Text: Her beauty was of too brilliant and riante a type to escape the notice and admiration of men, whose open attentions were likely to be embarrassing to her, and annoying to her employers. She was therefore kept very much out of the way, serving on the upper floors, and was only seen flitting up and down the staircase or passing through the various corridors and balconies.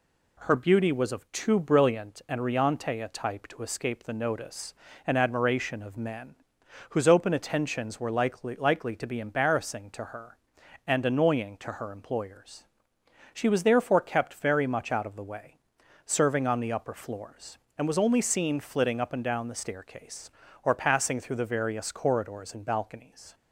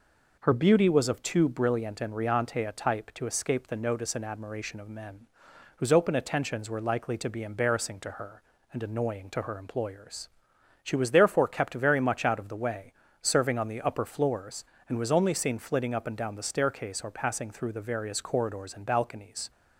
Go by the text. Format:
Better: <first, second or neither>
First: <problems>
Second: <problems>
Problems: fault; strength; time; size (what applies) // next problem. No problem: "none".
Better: second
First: says "likely" twice; at 8.5 s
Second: none